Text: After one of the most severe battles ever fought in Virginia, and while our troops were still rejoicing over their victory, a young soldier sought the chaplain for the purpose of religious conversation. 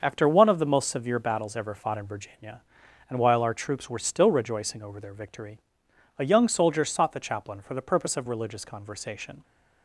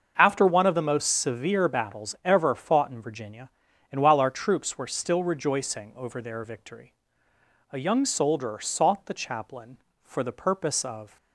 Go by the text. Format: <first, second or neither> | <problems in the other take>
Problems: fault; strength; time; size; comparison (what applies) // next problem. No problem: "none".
first | starts louder than the rest; until 1.1 s; 6.5 dB; also in the first // stops before "religious conversation"; at 11.1 s